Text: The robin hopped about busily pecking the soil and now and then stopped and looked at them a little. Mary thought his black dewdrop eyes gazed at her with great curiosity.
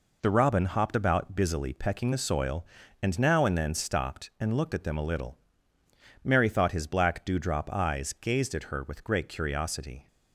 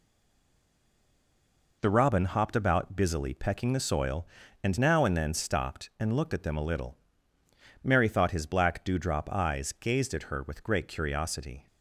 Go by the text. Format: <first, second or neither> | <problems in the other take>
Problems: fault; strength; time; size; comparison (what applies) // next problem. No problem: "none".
first | stays silent before the first word; noticeable; until 1.8 s; 1.8 s long